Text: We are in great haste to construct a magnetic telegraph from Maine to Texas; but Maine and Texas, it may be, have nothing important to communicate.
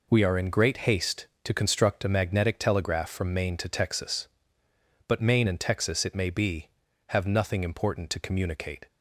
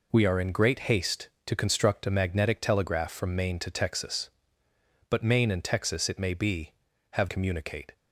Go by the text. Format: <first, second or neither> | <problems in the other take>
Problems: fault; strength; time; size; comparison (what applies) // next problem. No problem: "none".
first | skips "nothing important to"; at 7.2 s